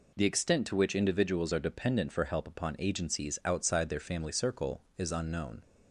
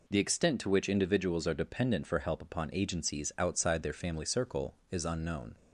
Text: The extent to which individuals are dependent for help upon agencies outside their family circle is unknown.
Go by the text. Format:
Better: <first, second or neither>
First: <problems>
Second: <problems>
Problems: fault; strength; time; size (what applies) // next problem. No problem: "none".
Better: neither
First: none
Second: none